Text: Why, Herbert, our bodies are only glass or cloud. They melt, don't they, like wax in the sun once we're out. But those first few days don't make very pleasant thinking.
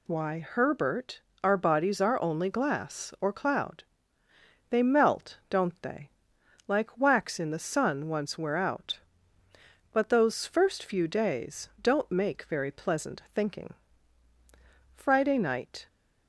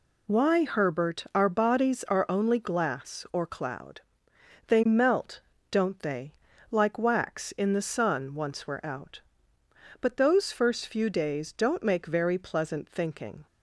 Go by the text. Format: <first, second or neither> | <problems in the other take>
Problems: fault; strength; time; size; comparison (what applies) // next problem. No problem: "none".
second | goes on to say "Friday night"; noticeable; from 14.9 s on; 0.92 s long